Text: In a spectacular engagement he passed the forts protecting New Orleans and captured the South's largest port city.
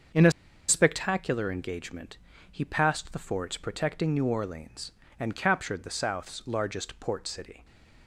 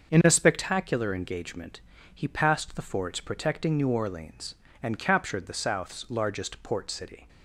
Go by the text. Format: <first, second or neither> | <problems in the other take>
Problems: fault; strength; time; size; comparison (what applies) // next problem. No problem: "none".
second | starts louder than the rest; until 1.5 s; 6.5 dB; also in the second // pauses between "a" and "spectacular"; at 0.3 s; 0.37 s long // pauses between "engagement" and "he"; slight; at 2.1 s; 0.32 s long; slight in the second // stays silent after the last word; slight; from 7.5 s on; 0.5 s long